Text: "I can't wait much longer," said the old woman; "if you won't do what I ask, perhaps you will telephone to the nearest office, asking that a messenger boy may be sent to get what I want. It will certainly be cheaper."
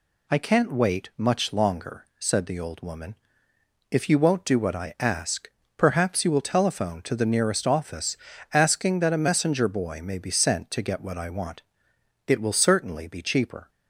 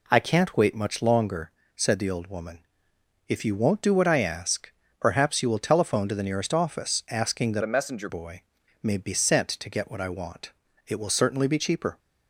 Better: first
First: none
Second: changes voice from "a" to "messenger"; from 7.6 to 8.0 s; 0.4 s long // pauses between "boy" and "may"; at 8.4 s; 0.38 s long

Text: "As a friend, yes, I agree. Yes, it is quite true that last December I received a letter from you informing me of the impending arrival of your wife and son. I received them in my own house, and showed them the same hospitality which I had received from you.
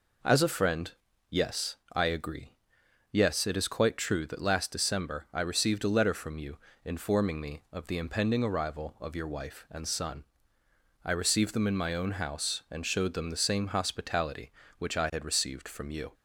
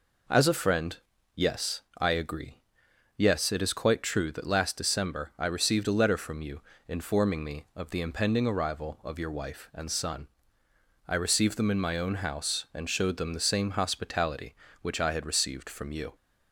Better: neither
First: pauses between "you" and "informing"; slight; at 6.5 s; 0.28 s long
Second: pauses between "you" and "informing"; slight; at 6.6 s; 0.28 s long

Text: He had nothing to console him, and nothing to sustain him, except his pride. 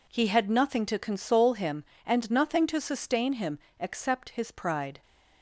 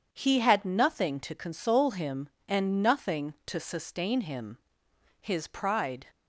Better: first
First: none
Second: skips "except"; at 4.8 s

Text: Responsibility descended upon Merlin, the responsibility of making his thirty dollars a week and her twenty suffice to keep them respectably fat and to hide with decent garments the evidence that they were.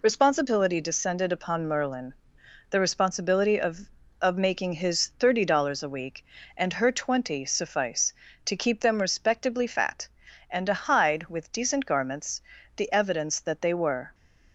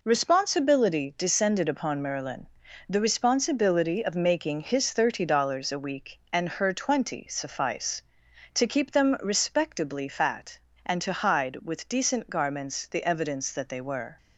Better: second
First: says "of" twice; at 4.2 s // pauses between "garments" and "the"; slight; at 12.4 s; 0.36 s long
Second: none

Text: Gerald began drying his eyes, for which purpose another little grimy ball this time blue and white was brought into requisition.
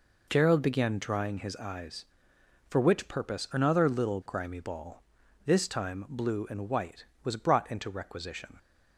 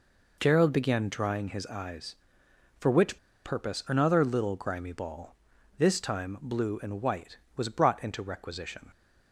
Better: first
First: pauses between "ball" and "this"; at 5.0 s; 0.42 s long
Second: pauses between "which" and "purpose"; slight; at 3.1 s; 0.26 s long // pauses between "ball" and "this"; at 5.3 s; 0.42 s long

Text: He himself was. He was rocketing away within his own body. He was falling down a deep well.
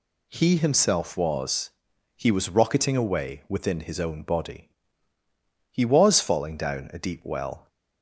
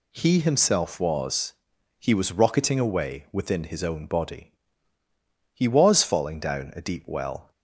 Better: neither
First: none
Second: none

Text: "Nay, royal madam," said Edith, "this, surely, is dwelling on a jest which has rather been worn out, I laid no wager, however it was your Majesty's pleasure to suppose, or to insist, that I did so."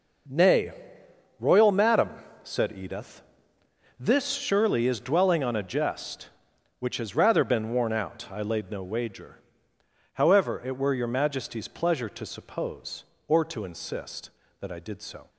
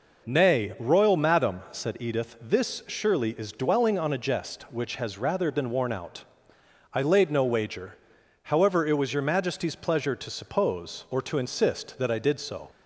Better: second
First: says "were" for "was"; at 10.7 s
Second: none

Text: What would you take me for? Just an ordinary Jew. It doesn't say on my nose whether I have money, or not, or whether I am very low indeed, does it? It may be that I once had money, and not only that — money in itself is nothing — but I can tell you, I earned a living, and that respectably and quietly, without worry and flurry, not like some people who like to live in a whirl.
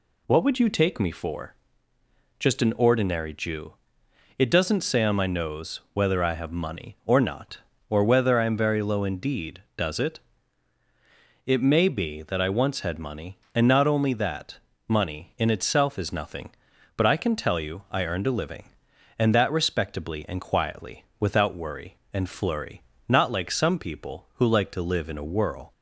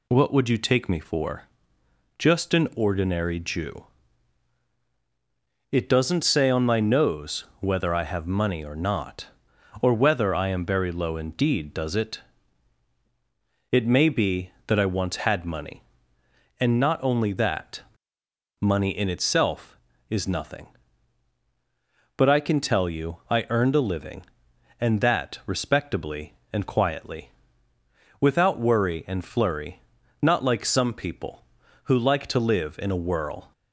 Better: neither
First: none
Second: none

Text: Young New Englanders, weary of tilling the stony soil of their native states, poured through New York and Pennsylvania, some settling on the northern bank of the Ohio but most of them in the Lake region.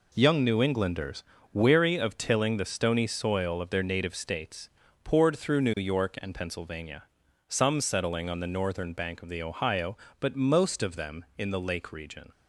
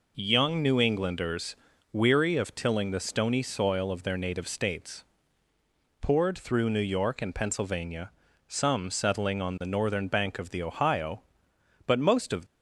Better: first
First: none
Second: stops before "them in the Lake region"; at 12.4 s

